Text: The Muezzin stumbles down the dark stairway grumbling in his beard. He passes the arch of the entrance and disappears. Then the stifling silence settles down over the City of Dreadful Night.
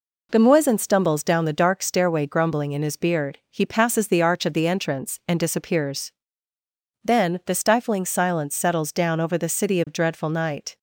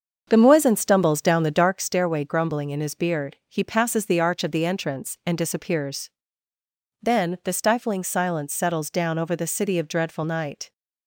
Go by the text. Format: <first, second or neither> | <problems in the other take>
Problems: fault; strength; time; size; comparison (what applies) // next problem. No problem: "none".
first | starts louder than the rest; until 1.8 s; 7 dB